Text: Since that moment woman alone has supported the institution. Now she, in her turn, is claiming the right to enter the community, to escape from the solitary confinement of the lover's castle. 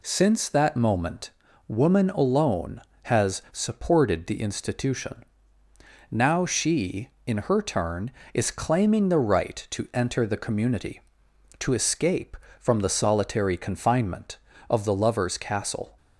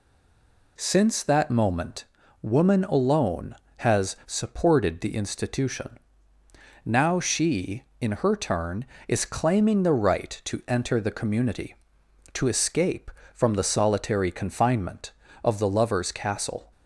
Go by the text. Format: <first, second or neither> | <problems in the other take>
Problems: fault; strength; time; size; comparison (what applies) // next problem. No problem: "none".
first | stays silent before the first word; slight; until 0.7 s; 0.7 s long // pauses between "moment" and "woman"; at 2.0 s; 0.38 s long; also in the first